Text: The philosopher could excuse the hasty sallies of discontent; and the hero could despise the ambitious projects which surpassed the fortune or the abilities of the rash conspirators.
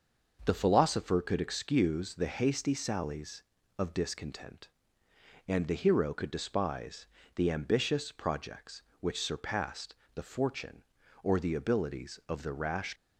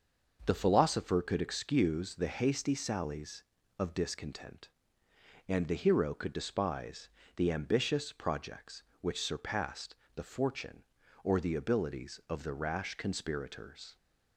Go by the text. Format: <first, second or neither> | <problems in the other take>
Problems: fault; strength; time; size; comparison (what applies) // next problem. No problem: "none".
second | starts louder than the rest; until 1.4 s; 6 dB; also in the second // pauses between "despise" and "the"; slight; at 7.0 s; 0.28 s long; slight in the second // pauses between "surpassed" and "the"; slight; at 9.9 s; 0.18 s long; slight in the second // stops before "conspirators"; at 12.9 s